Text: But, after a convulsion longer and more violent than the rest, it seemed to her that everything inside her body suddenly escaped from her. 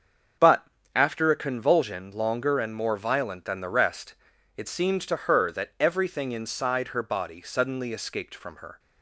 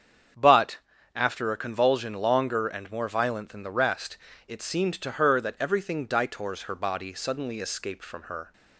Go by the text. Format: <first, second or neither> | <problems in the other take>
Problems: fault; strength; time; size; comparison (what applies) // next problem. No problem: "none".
first | starts louder than the rest; strong; until 1.7 s; 7.5 dB; also in the first // says "ditors" for "inside"; at 6.0 s